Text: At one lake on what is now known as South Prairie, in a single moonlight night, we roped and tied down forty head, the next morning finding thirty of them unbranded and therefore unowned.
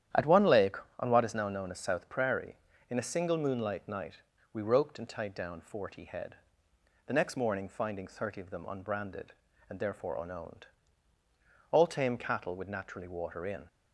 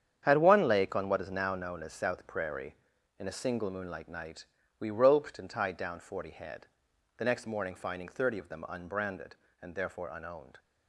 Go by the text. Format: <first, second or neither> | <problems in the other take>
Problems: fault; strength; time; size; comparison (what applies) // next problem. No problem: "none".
second | starts louder than the rest; strong; until 1.3 s; 10.5 dB; strong in the second // goes on to say "All tame cattle would naturally water in"; strong; from 11.7 s on; 1.9 s long